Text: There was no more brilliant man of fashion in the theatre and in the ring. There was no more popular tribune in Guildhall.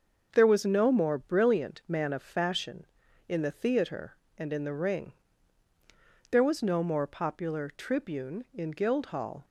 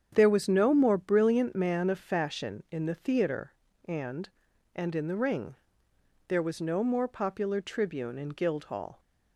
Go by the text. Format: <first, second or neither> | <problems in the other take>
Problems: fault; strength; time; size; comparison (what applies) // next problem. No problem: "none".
first | starts louder than the rest; strong; until 1.1 s; 8 dB; also in the first // says "and" twice; at 4.7 s